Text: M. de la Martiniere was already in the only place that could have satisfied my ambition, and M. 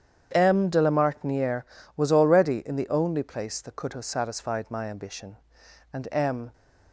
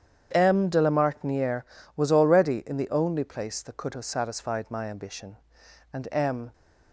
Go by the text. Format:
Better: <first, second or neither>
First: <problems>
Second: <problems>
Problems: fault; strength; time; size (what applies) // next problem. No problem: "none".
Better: neither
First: starts louder than the rest; strong; until 1.3 s; 8.5 dB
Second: starts louder than the rest; strong; until 1.3 s; 8.5 dB